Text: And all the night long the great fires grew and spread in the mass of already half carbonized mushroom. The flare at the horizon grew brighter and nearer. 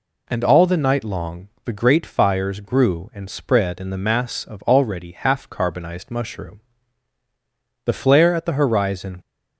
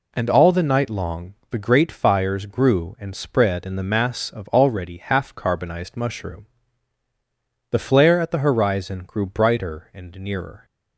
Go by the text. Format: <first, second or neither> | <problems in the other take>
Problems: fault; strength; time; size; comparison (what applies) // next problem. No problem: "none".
second | pauses between "long" and "the"; slight; at 1.4 s; 0.16 s long; slight in the second // stops before "grew brighter and nearer"; at 9.2 s